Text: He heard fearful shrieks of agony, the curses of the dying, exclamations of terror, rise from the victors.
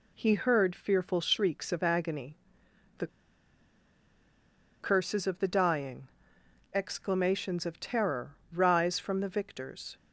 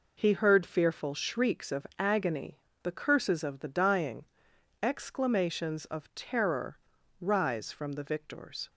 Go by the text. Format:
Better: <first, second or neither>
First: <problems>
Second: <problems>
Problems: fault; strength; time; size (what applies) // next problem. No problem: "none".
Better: second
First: pauses between "the" and "curses"; strong; at 3.0 s; 1.7 s long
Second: none